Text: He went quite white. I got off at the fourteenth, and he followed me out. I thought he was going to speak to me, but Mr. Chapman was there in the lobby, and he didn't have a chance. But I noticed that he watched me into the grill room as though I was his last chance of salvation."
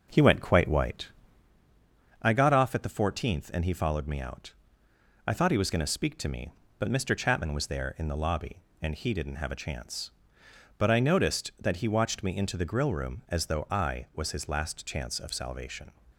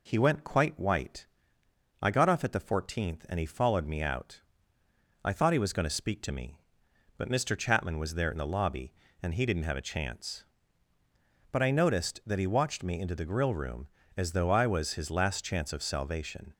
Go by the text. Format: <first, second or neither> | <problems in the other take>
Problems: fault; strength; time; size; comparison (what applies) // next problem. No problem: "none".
second | starts louder than the rest; noticeable; until 1.6 s; 5.5 dB